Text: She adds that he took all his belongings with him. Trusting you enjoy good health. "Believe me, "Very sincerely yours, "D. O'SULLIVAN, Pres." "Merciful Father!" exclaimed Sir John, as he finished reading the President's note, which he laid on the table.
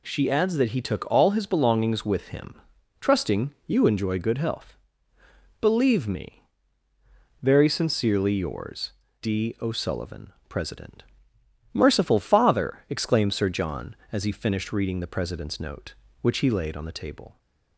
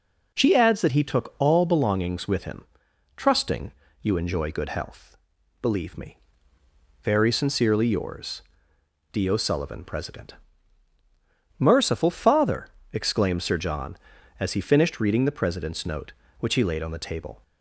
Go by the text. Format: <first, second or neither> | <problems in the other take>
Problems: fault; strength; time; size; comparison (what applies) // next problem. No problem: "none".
first | skips "his"; at 1.6 s // pauses between "Trusting" and "you"; slight; at 3.7 s; 0.30 s long